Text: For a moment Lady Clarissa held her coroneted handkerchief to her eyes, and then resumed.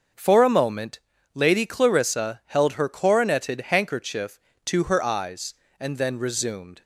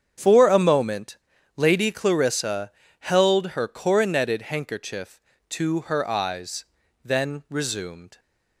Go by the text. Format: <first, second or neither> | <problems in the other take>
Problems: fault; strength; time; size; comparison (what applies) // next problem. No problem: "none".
first | starts louder than the rest; strong; until 1.5 s; 8 dB; also in the first // pauses between "moment" and "Lady"; at 1.1 s; 0.40 s long; slight in the first // pauses between "Clarissa" and "held"; slight; at 2.6 s; 0.30 s long // skips "and"; at 6.8 s